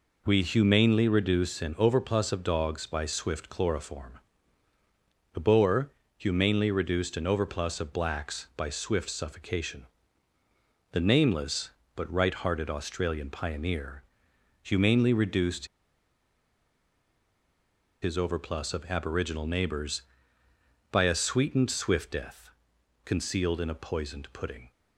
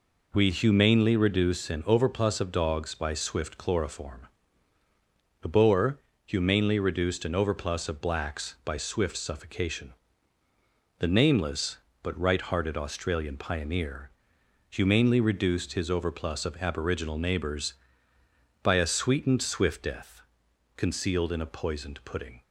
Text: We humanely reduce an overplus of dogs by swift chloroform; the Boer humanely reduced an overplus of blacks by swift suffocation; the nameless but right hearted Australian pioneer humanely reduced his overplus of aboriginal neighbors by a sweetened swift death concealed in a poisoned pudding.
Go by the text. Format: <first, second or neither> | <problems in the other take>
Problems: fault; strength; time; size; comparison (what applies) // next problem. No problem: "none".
second | pauses between "Boer" and "humanely"; slight; at 5.8 s; 0.26 s long; slight in the second // pauses between "pioneer" and "humanely"; noticeable; at 14.0 s; 0.60 s long; noticeable in the second // pauses between "reduced" and "his"; strong; at 15.6 s; 2.3 s long // pauses between "death" and "concealed"; noticeable; at 22.5 s; 0.54 s long; noticeable in the second